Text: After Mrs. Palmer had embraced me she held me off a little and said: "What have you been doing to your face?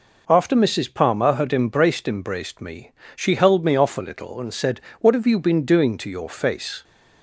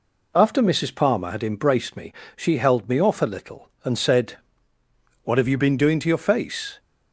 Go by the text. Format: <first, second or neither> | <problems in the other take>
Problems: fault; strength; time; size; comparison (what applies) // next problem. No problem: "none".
second | says "embraced" twice; at 2.0 s // pauses between "me" and "she"; slight; at 2.9 s; 0.24 s long; slight in the second